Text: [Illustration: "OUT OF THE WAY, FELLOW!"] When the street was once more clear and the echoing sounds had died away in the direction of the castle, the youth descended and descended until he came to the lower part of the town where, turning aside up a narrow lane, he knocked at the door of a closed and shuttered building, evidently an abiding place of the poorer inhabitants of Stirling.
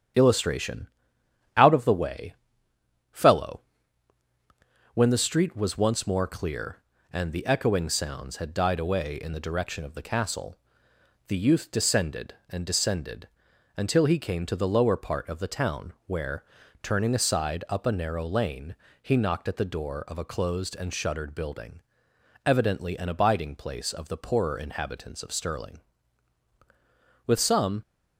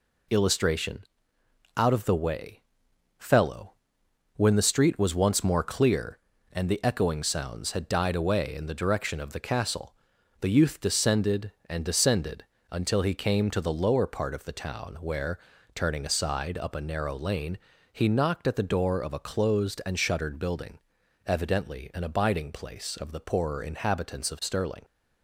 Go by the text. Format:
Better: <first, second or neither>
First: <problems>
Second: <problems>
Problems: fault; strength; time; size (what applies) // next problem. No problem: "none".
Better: second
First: starts louder than the rest; strong; until 1.8 s; 8.5 dB // pauses between "descended" and "until"; noticeable; at 13.2 s; 0.48 s long // goes on to say "With some"; from 27.2 s on; 0.56 s long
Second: pauses between "descended" and "until"; slight; at 12.4 s; 0.26 s long